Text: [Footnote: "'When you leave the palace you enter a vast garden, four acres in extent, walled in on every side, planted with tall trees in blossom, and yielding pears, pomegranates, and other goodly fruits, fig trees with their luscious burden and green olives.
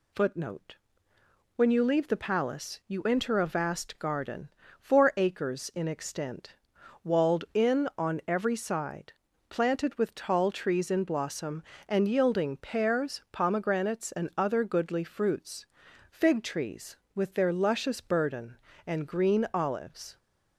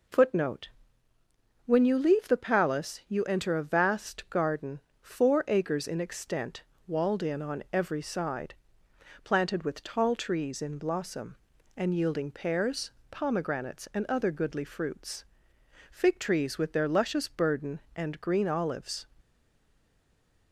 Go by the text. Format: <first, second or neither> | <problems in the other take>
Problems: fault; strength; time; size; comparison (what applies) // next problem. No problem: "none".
first | stays silent after the last word; noticeable; from 19.1 s on; 1.4 s long